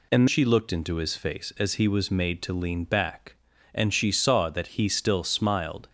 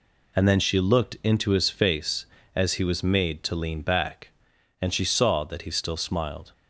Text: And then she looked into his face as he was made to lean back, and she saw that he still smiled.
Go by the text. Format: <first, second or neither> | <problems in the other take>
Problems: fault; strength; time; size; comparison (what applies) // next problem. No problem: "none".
second | skips "then"; at 0.2 s